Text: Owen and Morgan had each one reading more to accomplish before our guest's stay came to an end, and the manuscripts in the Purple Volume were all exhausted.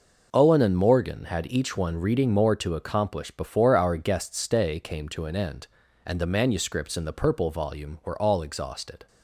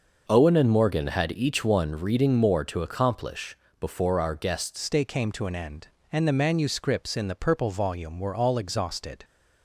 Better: first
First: none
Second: pauses between "accomplish" and "before"; slight; at 3.5 s; 0.22 s long // changes voice at "stay"; from 4.7 s on; 4.5 s long

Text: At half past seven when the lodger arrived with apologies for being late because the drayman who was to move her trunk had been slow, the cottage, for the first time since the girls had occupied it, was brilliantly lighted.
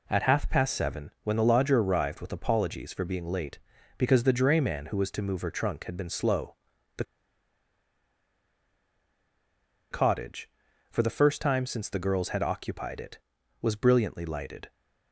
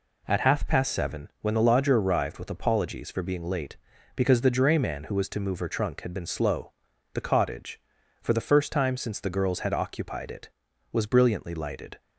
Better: second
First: pauses between "the" and "cottage"; strong; at 7.0 s; 2.8 s long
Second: none

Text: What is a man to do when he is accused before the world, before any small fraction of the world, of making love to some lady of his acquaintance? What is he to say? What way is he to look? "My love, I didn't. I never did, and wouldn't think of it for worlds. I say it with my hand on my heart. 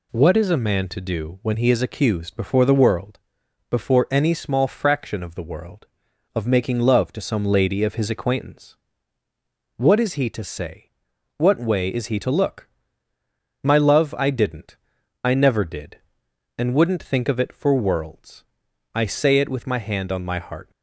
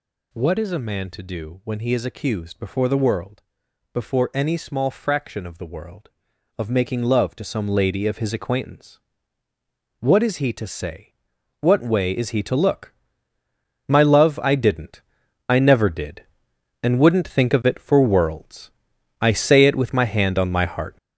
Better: first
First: none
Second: gets louder; throughout; 7 dB

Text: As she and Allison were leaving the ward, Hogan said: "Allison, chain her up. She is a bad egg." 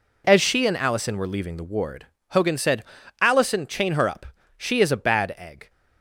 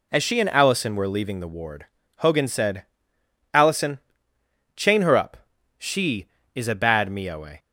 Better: first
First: none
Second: says "mioe" for "egg"; at 7.0 s

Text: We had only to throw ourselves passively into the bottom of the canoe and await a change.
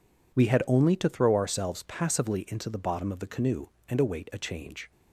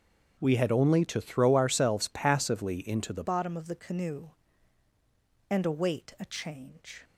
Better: first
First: none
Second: starts louder than the rest; strong; until 1.4 s; 7 dB // changes voice at "bottom"; from 3.2 s on; 3.8 s long

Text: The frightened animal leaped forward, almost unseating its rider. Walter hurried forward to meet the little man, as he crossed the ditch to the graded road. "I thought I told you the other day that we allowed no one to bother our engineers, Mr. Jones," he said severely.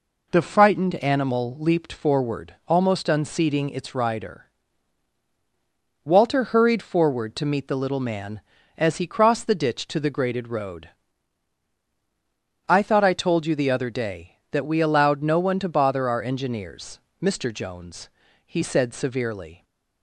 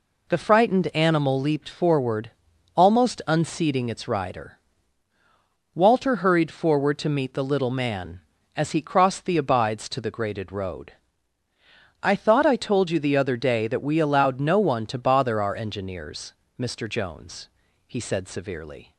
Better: first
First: none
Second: says "abides" for "ditch"; at 9.3 s

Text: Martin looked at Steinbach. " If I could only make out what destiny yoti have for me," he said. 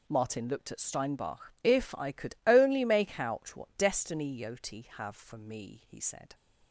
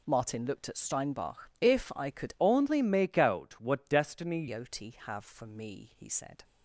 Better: first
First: none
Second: changes voice from "only" to "destiny"; from 2.4 to 4.4 s; 2.0 s long

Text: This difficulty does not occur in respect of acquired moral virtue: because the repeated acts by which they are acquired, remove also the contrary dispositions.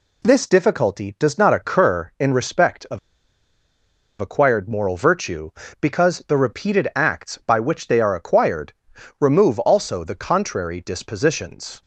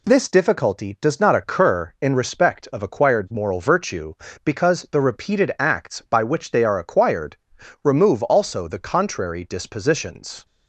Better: second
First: pauses between "of" and "acquired"; at 2.9 s; 1.2 s long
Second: none

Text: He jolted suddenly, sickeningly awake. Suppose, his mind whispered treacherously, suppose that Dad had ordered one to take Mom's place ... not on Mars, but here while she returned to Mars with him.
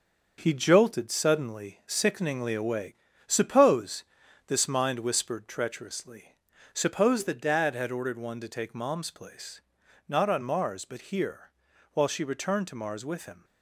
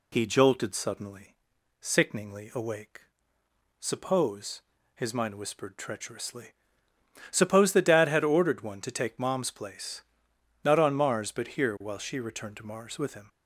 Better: second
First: starts louder than the rest; until 1.3 s; 6.5 dB // says "this" for "his"; at 4.4 s // pauses between "here" and "while"; at 11.5 s; 0.44 s long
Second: none

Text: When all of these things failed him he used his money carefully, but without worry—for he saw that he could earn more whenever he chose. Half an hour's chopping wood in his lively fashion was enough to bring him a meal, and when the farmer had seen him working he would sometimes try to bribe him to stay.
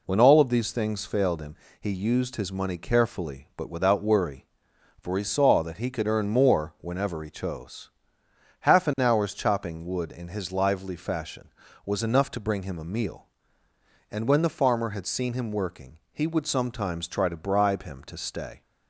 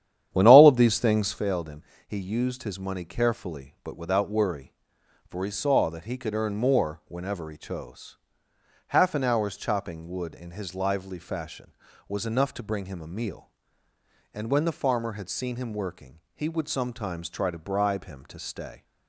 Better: first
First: pauses between "him" and "he"; slight; at 1.5 s; 0.24 s long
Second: starts louder than the rest; strong; until 1.4 s; 10 dB // pauses between "him" and "he"; slight; at 1.8 s; 0.24 s long

